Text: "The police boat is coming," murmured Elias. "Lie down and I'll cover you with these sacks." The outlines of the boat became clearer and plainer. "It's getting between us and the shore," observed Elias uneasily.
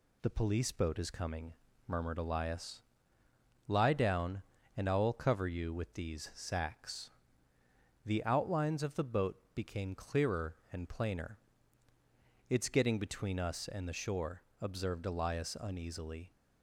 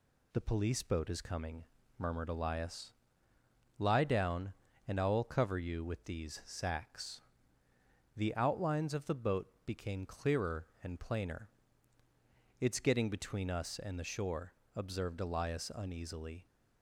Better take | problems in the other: neither | none

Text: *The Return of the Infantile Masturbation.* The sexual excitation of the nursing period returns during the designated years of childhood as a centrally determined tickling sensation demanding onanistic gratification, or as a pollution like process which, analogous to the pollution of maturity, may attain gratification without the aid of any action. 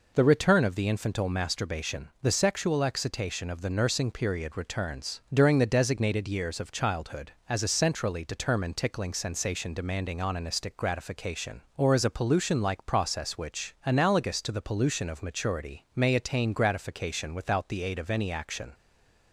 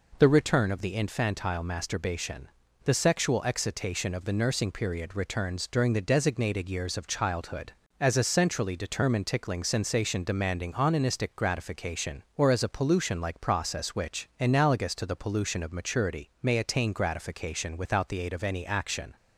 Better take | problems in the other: second | stays silent after the last word; slight; from 18.7 s on; 0.6 s long

